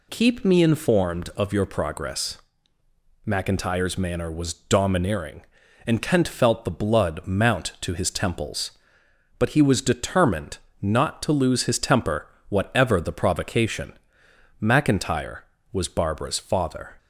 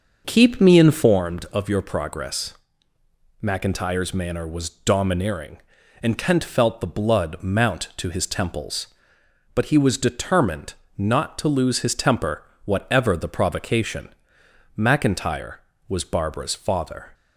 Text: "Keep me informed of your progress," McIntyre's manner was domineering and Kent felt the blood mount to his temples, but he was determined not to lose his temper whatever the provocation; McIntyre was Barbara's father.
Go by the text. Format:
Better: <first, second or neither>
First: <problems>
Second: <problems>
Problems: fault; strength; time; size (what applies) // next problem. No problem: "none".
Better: first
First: pauses between "determined" and "not"; slight; at 10.5 s; 0.24 s long // pauses between "temper" and "whatever"; slight; at 12.2 s; 0.20 s long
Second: starts louder than the rest; noticeable; until 1.2 s; 6 dB // pauses between "determined" and "not"; slight; at 10.7 s; 0.24 s long // pauses between "temper" and "whatever"; slight; at 12.4 s; 0.20 s long